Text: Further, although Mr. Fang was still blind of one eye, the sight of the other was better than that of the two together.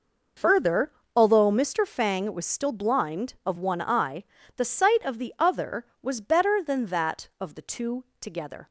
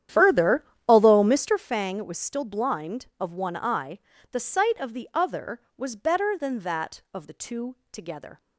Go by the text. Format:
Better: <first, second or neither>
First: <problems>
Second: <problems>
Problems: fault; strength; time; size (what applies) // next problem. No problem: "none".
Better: first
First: pauses between "two" and "together"; slight; at 8.0 s; 0.16 s long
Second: starts louder than the rest; strong; until 1.7 s; 10 dB // pauses between "two" and "together"; slight; at 7.7 s; 0.16 s long